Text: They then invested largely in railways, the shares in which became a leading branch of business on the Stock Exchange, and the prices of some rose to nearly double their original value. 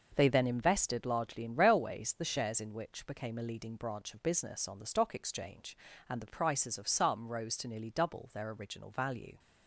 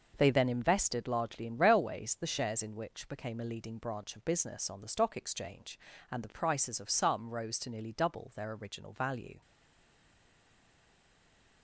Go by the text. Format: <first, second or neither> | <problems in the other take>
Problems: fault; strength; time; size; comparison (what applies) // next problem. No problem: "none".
first | stays silent after the last word; from 9.4 s on; 2.2 s long